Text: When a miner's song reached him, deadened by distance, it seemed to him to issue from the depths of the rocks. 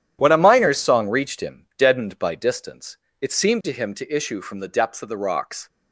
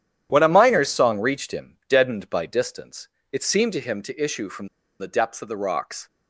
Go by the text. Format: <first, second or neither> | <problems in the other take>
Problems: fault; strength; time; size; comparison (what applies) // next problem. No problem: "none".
first | starts louder than the rest; strong; until 1.3 s; 10.5 dB; strong in the first // pauses between "from" and "the"; slight; at 4.6 s; 0.32 s long